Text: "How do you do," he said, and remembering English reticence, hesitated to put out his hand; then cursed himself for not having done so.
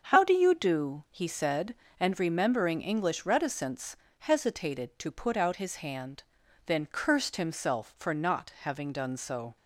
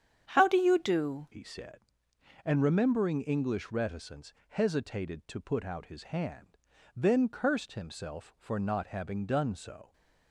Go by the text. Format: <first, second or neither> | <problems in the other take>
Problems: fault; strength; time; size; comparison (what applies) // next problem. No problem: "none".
first | starts louder than the rest; strong; until 1.3 s; 8.5 dB; also in the first // changes voice at "he"; from 1.3 s on; 8.6 s long